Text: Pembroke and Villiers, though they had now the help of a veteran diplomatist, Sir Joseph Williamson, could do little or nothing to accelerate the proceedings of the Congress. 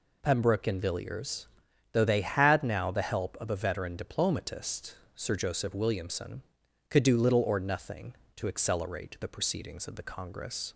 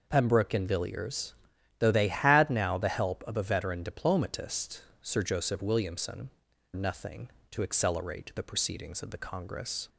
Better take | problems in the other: first | skips "could do little or"; at 6.5 s

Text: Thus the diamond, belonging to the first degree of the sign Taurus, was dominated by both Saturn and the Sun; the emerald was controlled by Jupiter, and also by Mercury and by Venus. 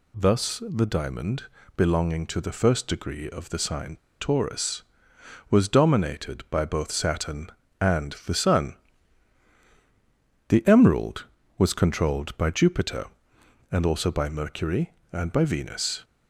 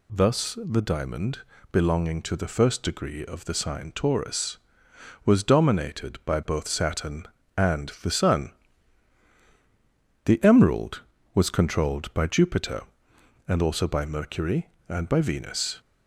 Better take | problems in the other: second | pauses between "sign" and "Taurus"; slight; at 3.9 s; 0.22 s long

